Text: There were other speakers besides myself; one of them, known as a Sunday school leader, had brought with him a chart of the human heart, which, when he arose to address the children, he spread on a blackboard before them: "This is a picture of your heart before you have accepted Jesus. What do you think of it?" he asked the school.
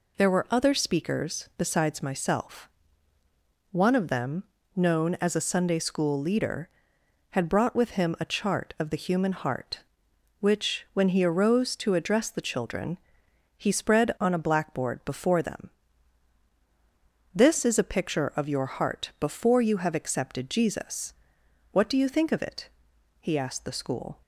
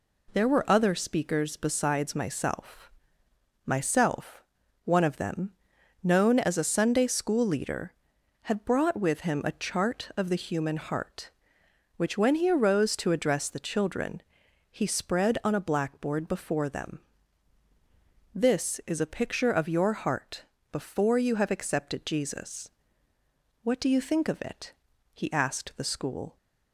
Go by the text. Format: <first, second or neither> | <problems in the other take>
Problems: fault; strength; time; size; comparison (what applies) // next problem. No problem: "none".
first | says "myself" twice; at 3.6 s // pauses between "heart" and "before"; slight; at 20.4 s; 0.26 s long